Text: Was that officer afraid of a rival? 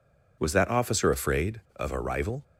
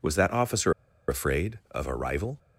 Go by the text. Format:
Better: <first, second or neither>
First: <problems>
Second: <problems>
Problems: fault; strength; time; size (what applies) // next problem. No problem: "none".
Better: first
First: none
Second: pauses between "officer" and "afraid"; slight; at 0.7 s; 0.35 s long